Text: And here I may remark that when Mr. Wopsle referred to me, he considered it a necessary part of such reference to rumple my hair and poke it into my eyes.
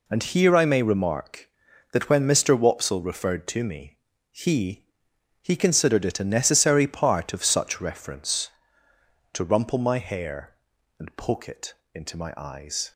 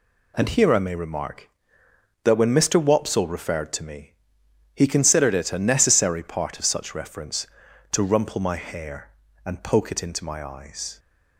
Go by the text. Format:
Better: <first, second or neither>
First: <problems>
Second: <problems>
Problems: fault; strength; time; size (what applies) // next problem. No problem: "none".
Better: second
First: says "he" twice; at 5.4 s // pauses between "it" and "into"; slight; at 11.7 s; 0.20 s long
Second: none